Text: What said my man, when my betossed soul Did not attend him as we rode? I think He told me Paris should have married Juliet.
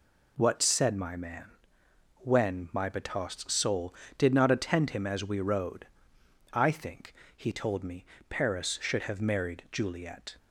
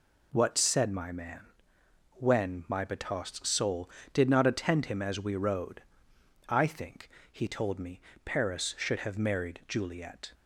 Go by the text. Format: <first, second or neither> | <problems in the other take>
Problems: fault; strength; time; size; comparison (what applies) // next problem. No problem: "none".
neither | pauses between "think" and "He"; slight; the same in both // pauses between "me" and "Paris"; slight; the same in both